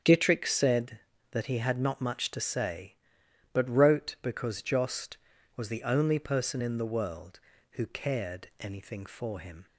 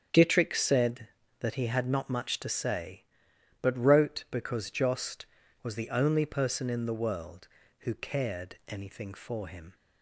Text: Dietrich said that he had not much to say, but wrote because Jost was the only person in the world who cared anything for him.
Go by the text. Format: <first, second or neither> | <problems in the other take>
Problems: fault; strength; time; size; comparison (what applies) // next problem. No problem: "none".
neither | starts louder than the rest; strong; the same in both